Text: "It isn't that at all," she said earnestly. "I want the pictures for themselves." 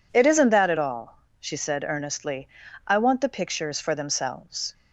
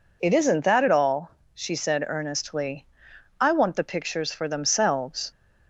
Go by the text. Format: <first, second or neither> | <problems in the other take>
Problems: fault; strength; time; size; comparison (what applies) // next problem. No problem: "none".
neither | none